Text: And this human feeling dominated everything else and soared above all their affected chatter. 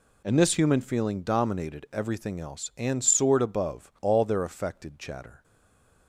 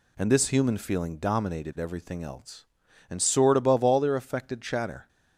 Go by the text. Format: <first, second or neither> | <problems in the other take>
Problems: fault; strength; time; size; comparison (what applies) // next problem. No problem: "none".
second | stays silent after the last word; slight; from 5.4 s on; 0.6 s long